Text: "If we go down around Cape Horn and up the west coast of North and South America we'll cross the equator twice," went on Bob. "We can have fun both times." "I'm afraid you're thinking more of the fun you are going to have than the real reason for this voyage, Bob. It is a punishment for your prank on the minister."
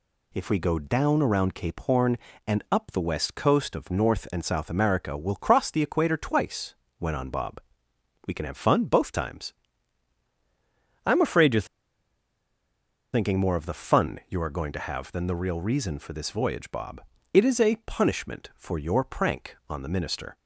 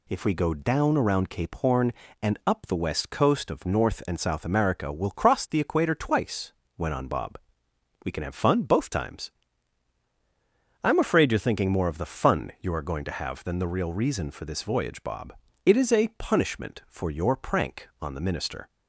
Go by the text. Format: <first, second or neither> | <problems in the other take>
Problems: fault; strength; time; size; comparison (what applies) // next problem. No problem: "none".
second | pauses between "you're" and "thinking"; strong; at 11.6 s; 1.4 s long